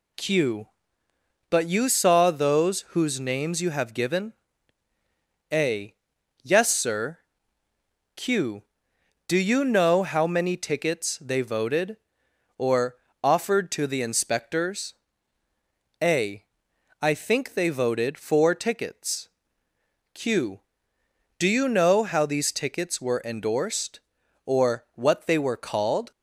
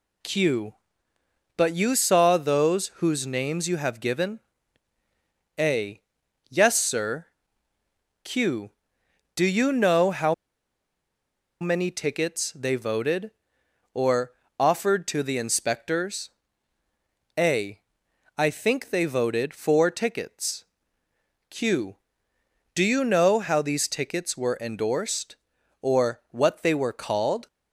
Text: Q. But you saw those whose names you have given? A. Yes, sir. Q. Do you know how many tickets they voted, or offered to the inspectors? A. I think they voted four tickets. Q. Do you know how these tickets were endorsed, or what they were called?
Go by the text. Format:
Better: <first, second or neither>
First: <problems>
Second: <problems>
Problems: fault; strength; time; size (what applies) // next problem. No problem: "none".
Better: first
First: pauses between "or" and "offered"; slight; at 12.9 s; 0.28 s long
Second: pauses between "how" and "many"; strong; at 10.3 s; 1.2 s long // pauses between "or" and "offered"; slight; at 14.3 s; 0.28 s long